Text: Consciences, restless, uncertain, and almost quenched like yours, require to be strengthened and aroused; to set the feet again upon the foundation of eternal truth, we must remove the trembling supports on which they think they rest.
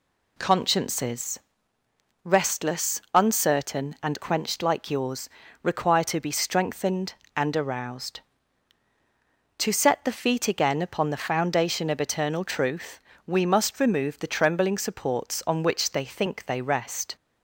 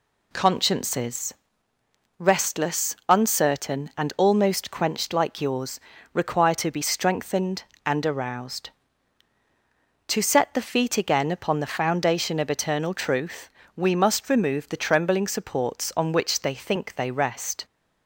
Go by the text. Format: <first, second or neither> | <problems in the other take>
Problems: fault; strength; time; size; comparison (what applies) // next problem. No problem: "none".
second | skips "almost"; at 4.2 s